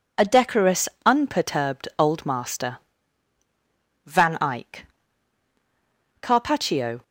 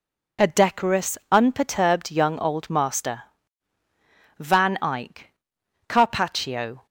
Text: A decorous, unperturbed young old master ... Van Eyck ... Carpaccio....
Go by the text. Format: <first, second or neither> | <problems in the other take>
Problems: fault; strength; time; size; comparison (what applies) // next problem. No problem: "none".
second | skips "young"; at 1.9 s